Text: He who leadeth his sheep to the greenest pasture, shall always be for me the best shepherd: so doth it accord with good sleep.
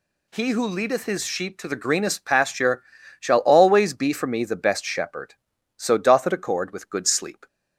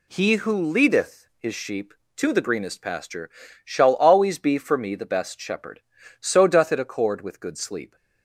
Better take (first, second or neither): neither